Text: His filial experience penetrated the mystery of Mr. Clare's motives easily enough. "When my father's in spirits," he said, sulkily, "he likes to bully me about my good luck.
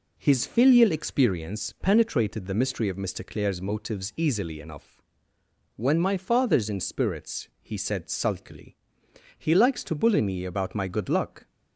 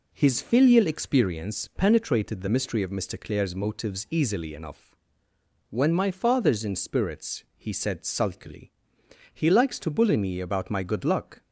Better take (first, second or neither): neither